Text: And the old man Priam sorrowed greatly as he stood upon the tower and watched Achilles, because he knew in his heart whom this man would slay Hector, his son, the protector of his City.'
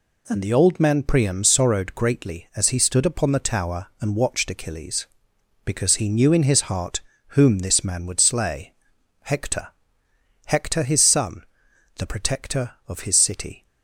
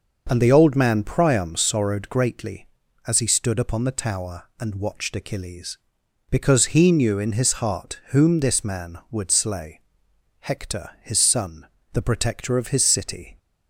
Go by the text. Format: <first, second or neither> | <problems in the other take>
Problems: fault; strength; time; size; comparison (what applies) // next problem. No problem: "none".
second | pauses between "heart" and "whom"; slight; at 7.0 s; 0.28 s long // pauses between "slay" and "Hector"; noticeable; at 8.7 s; 0.50 s long; noticeable in the second // says "Hector" twice; at 10.4 s